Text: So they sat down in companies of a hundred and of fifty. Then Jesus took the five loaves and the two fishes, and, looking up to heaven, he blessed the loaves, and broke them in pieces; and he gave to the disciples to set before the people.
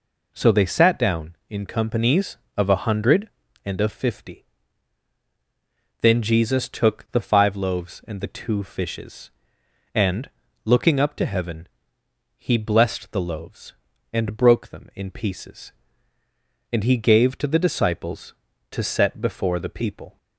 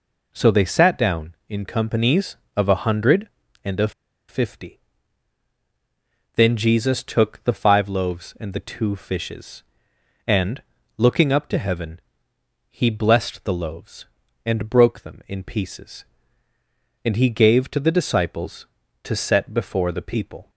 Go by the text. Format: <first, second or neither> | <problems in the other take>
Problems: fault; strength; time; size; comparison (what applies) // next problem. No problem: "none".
first | pauses between "of" and "fifty"; at 3.9 s; 0.38 s long